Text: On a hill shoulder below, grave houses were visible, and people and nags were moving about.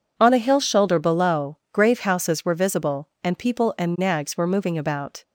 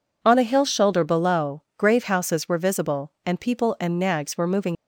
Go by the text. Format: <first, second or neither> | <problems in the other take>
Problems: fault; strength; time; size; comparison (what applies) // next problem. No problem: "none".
first | stops before "about"; at 4.7 s